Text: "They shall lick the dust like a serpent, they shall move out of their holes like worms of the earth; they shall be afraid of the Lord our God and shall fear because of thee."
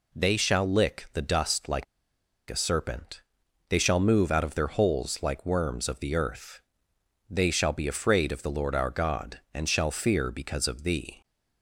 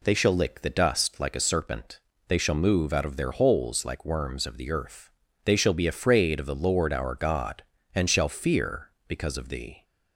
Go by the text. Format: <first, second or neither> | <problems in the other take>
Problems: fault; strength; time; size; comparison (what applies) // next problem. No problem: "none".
second | pauses between "like" and "a"; noticeable; at 1.8 s; 0.65 s long